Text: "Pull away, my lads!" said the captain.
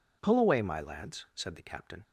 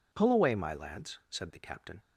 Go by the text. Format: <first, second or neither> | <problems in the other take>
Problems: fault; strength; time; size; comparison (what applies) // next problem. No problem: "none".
neither | none